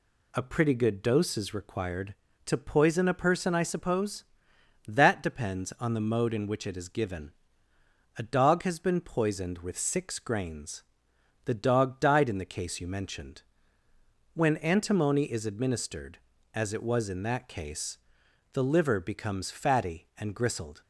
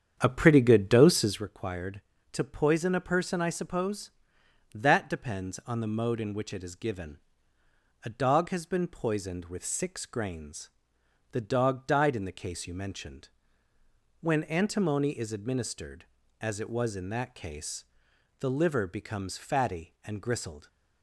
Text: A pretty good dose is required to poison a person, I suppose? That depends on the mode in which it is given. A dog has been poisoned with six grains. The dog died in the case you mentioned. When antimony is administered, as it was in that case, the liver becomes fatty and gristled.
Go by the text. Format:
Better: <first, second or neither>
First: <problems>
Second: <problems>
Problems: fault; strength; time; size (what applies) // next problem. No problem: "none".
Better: first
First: none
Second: starts louder than the rest; strong; until 1.5 s; 8.5 dB